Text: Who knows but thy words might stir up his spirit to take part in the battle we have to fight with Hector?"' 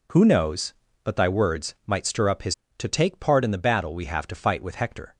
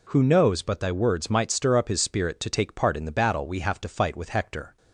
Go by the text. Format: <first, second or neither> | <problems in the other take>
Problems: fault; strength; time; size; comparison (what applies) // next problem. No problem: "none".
second | skips "spirit"; at 2.6 s